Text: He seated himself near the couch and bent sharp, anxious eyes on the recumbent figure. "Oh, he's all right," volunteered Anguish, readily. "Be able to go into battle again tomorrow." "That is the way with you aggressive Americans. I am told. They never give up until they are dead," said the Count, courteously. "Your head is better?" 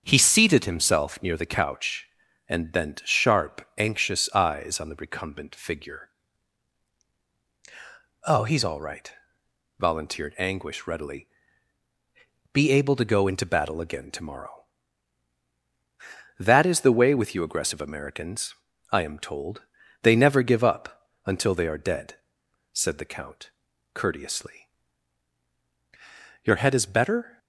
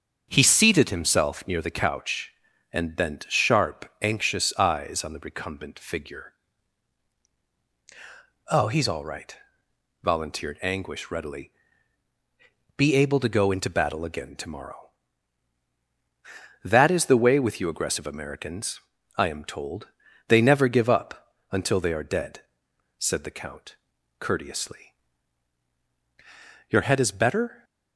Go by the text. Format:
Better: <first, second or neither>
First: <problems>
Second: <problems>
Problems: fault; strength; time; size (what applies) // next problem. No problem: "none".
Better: neither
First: starts louder than the rest; until 1.0 s; 6.5 dB // pauses between "up" and "until"; slight; at 21.1 s; 0.16 s long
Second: starts louder than the rest; until 1.3 s; 6.5 dB // pauses between "up" and "until"; slight; at 21.3 s; 0.16 s long